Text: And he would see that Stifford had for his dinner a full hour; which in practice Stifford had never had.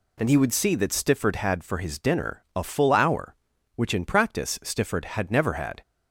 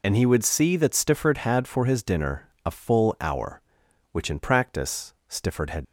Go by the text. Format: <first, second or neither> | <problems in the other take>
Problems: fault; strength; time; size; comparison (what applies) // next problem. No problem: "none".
first | pauses between "dinner" and "a"; slight; at 2.4 s; 0.16 s long // pauses between "practice" and "Stifford"; slight; at 5.1 s; 0.16 s long // stops before "never had"; at 5.8 s